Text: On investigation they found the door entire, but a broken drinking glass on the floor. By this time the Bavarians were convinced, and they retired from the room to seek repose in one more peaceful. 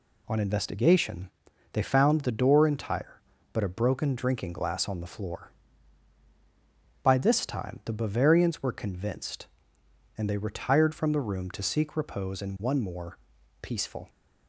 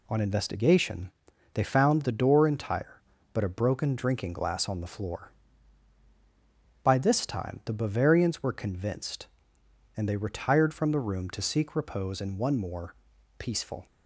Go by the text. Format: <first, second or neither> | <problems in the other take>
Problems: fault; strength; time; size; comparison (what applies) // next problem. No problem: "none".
neither | pauses between "investigation" and "they"; the same in both // pauses between "more" and "peaceful"; the same in both